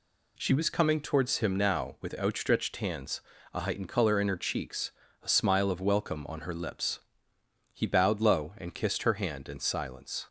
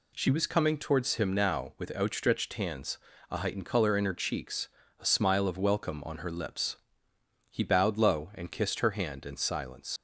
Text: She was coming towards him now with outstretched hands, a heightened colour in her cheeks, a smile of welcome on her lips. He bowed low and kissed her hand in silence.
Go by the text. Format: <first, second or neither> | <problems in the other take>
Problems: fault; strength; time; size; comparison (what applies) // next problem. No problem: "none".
first | leaves "silence" unfinished; at 9.9 s; 80 ms